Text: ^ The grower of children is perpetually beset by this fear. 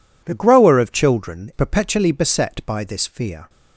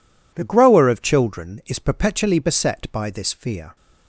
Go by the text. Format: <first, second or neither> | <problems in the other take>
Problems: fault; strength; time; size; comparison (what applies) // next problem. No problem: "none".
second | skips "is"; at 1.5 s